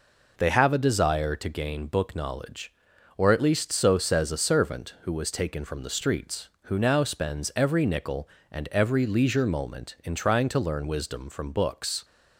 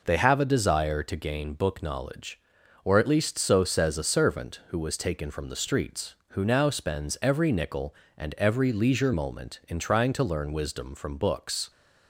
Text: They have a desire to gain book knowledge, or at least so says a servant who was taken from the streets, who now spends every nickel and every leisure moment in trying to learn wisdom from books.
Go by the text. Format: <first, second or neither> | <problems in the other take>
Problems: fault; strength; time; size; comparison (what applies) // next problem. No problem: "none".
neither | none